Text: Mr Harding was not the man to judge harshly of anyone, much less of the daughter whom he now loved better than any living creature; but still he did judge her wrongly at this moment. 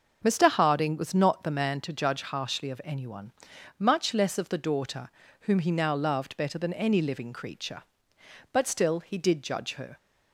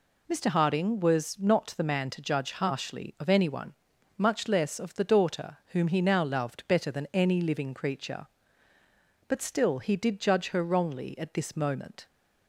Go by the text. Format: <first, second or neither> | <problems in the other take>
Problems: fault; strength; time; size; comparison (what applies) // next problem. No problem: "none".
second | starts louder than the rest; noticeable; until 1.2 s; 6 dB // pauses between "daughter" and "whom"; slight; at 5.1 s; 0.32 s long // stops before "wrongly at this moment"; at 9.9 s